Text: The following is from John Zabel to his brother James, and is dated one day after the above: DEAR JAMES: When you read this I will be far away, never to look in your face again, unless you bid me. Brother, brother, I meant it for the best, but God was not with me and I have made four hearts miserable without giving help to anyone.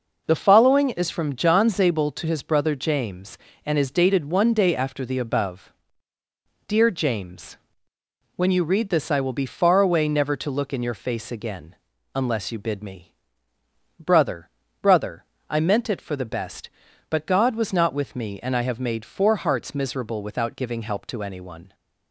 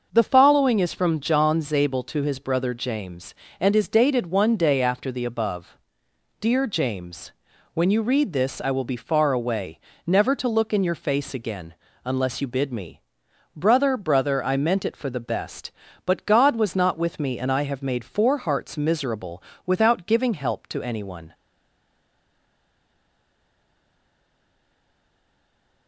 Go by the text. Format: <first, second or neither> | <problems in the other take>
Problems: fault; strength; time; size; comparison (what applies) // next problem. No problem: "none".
first | starts louder than the rest; until 1.1 s; 6.5 dB // pauses between "miserable" and "without"; slight; at 19.3 s; 0.24 s long // stays silent after the last word; strong; from 21.3 s on; 4.5 s long